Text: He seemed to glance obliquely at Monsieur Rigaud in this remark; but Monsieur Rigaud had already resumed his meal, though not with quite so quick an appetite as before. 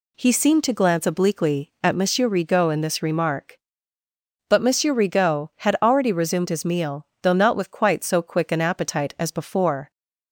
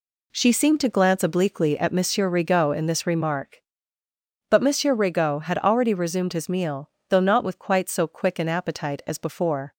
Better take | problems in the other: first | says "She" for "He"; at 0.3 s

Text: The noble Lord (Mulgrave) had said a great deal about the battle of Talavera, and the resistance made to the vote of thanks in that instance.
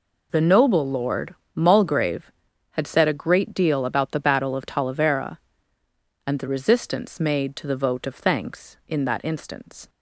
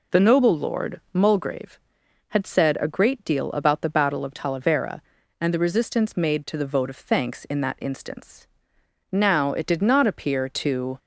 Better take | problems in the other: first | goes on to say "Now it did not appear to"; strong; from 9.1 s on; 1.8 s long

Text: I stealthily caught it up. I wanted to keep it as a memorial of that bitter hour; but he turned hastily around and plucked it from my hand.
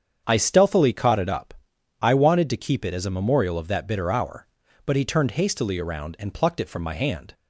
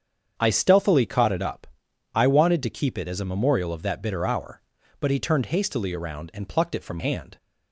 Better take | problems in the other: first | starts louder than the rest; strong; until 1.3 s; 7.5 dB; strong in the first // skips "my"; at 6.9 s

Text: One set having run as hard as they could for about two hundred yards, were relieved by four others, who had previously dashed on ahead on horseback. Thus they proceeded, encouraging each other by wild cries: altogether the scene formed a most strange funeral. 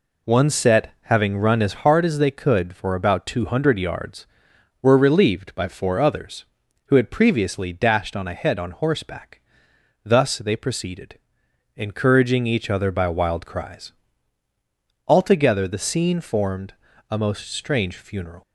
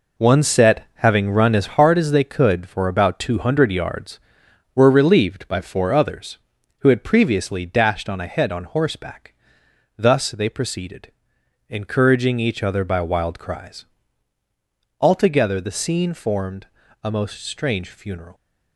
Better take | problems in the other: first | gets quieter; strong; throughout; 7 dB // pauses between "formed" and "a"; slight; at 16.6 s; 0.36 s long; slight in the first

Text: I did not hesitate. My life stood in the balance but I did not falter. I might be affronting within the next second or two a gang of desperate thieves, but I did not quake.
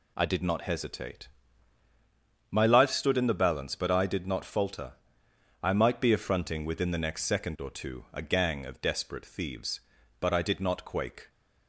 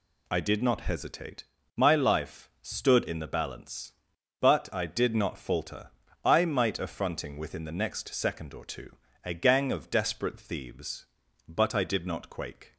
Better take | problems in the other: first | skips "be"; at 6.7 s // pauses between "two" and "a"; slight; at 8.9 s; 0.32 s long

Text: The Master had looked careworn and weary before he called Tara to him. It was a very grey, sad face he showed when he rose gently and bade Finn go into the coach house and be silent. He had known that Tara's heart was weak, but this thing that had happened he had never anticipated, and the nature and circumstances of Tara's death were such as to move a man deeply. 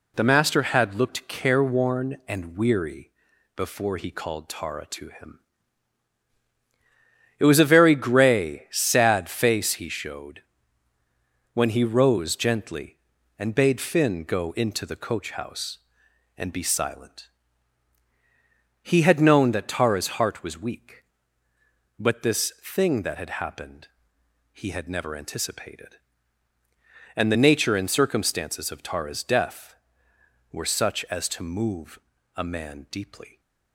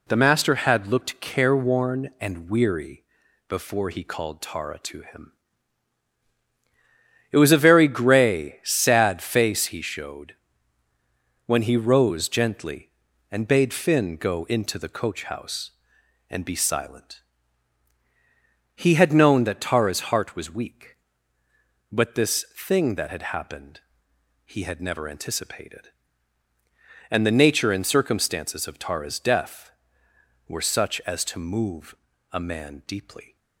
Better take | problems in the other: neither | pauses between "weary" and "before"; noticeable; the same in both // pauses between "showed" and "when"; the same in both // pauses between "happened" and "he"; noticeable; the same in both // pauses between "move" and "a"; the same in both

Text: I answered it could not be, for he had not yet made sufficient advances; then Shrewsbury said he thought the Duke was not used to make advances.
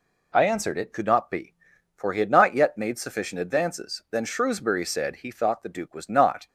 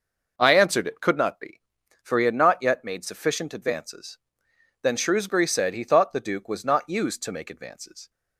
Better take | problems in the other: second | stops before "used to make advances"; at 6.4 s

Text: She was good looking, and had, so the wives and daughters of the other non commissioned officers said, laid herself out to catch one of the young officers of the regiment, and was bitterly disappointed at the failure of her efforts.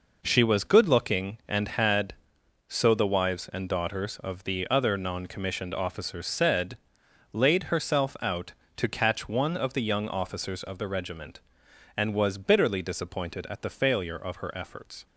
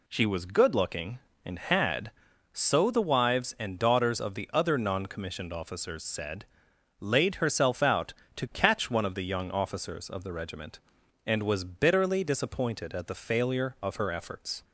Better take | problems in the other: neither | none

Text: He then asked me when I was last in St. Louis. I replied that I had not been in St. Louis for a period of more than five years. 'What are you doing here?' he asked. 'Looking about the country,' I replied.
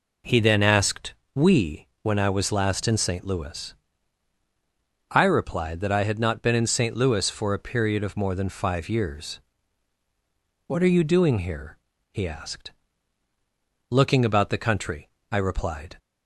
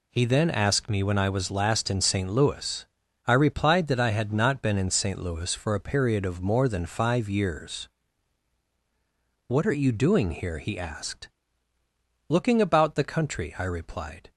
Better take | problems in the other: second | says "we" for "me"; at 1.3 s

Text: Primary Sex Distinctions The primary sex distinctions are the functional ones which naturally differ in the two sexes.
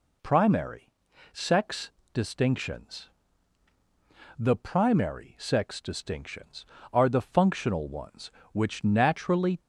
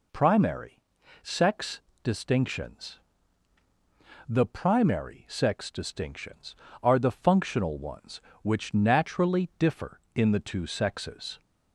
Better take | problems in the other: second | pauses between "Primary" and "Sex"; at 0.8 s; 0.44 s long; also in the second // pauses between "Sex" and "Distinctions"; slight; at 1.8 s; 0.24 s long; slight in the second // pauses between "Distinctions" and "The"; strong; at 3.0 s; 1.2 s long; strong in the second // stops before "differ in the two sexes"; at 9.5 s

